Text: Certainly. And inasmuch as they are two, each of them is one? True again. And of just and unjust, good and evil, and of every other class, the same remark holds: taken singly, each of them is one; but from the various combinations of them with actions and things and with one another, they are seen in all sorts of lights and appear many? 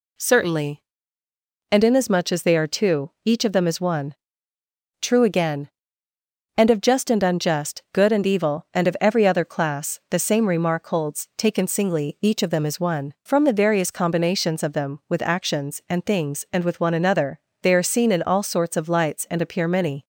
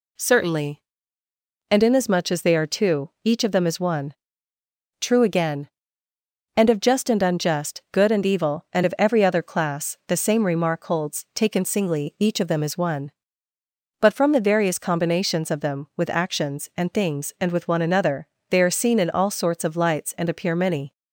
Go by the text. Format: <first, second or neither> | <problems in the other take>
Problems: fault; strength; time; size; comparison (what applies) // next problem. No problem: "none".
second | skips "but"; at 13.1 s